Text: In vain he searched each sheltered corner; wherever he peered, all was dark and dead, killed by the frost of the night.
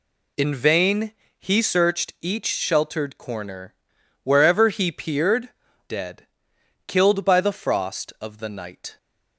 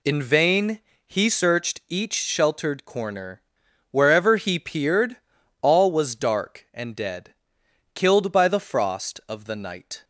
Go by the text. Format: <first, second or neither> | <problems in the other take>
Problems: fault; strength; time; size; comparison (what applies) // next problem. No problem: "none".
second | pauses between "vain" and "he"; slight; at 1.1 s; 0.26 s long; slight in the second // skips "all was dark and"; at 5.6 s